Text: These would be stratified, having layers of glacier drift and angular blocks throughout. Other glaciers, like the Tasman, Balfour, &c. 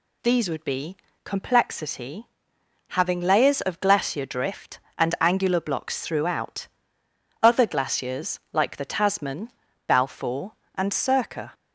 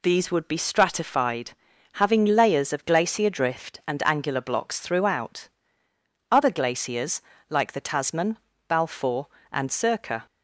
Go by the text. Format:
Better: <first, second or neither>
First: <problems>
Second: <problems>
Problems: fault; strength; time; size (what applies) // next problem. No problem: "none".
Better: second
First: says "complexity" for "stratified"; at 1.2 s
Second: none